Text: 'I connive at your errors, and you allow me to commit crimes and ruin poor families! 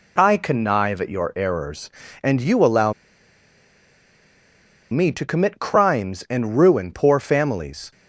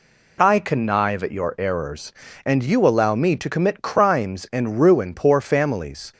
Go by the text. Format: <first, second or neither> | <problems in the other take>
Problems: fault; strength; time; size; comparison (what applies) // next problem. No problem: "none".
second | pauses between "allow" and "me"; strong; at 2.9 s; 2.0 s long